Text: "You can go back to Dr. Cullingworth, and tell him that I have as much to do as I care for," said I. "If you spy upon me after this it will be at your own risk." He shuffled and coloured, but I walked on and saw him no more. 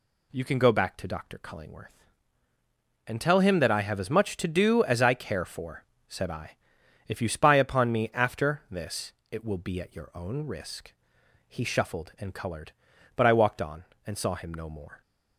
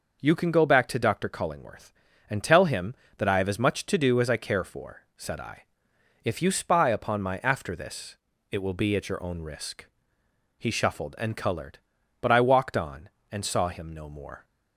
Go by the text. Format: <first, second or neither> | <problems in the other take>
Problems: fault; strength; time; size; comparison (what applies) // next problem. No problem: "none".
first | says "my" for "me"; at 7.2 s // pauses between "this" and "it"; slight; at 8.1 s; 0.34 s long; slight in the first